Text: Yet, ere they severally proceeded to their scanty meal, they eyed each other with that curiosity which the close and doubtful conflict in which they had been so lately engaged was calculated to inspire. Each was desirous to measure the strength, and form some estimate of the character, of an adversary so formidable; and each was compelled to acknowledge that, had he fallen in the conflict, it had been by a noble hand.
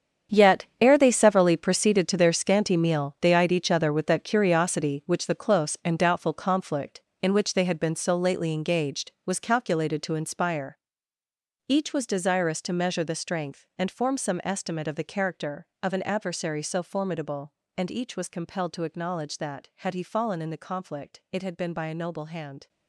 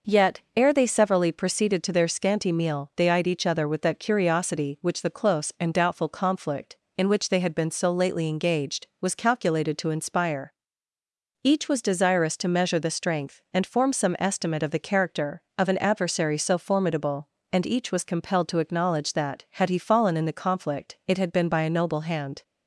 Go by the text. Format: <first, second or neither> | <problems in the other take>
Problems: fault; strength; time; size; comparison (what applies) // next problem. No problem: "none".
second | gets quieter; strong; throughout; 13 dB